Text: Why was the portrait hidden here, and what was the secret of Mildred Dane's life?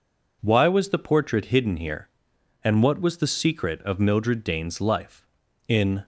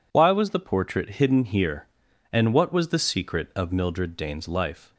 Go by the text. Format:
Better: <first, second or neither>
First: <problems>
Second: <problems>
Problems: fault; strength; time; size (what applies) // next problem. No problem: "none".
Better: second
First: goes on to say "In"; slight; from 5.6 s on; 0.36 s long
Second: none